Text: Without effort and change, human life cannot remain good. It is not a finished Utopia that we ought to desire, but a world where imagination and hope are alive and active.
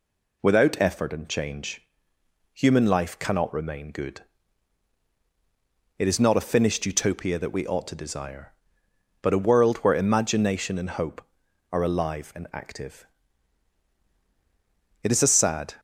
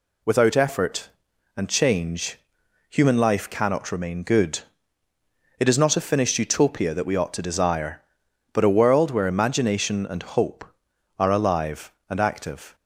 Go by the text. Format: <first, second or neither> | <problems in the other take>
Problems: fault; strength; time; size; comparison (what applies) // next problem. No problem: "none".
second | goes on to say "It is a sad"; noticeable; from 15.0 s on; 0.74 s long